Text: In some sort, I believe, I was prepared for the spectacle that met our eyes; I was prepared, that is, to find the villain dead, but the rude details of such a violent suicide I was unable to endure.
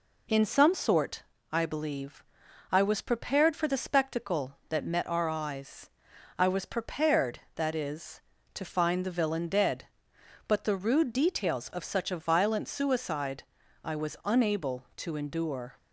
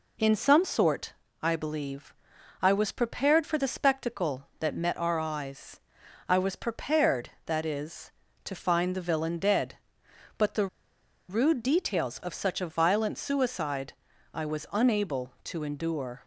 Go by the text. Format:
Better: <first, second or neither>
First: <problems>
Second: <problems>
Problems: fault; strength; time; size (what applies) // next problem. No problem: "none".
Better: first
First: pauses between "suicide" and "I"; at 13.4 s; 0.40 s long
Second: pauses between "the" and "rude"; noticeable; at 10.6 s; 0.62 s long // pauses between "suicide" and "I"; at 13.9 s; 0.40 s long